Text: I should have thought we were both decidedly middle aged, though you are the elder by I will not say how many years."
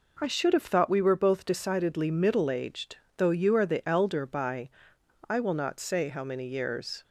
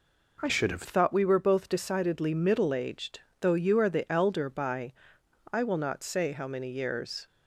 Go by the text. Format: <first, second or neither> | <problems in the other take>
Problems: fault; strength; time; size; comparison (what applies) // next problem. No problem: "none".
first | changes voice from "should" to "have"; from 0.4 to 0.8 s; 0.4 s long // pauses between "by" and "I"; noticeable; at 4.9 s; 0.60 s long; noticeable in the first